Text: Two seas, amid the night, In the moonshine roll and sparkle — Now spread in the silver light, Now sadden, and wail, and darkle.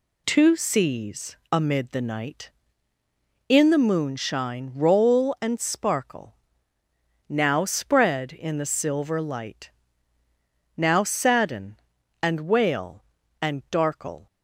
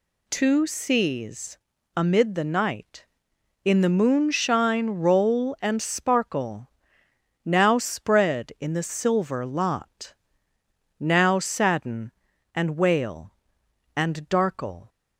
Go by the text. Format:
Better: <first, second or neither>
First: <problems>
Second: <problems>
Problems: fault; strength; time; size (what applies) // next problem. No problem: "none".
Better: first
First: none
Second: says "lot" for "light"; at 9.4 s